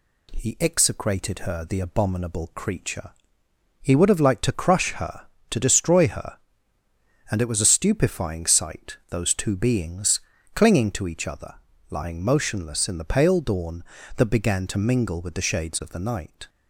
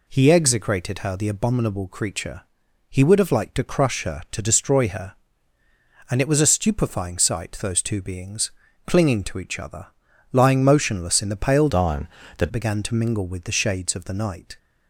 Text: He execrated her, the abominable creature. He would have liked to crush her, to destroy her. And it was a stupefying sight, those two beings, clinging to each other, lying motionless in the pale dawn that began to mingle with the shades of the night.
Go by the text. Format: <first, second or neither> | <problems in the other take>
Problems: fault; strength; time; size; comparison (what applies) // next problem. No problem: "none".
first | changes voice from "dawn" to "that"; from 11.6 to 12.5 s; 0.9 s long